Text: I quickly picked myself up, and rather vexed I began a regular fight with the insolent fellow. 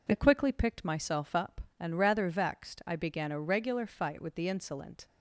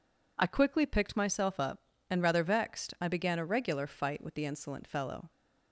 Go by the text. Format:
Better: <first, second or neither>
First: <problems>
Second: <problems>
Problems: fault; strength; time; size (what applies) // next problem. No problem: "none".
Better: second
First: stops before "fellow"; at 5.0 s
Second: none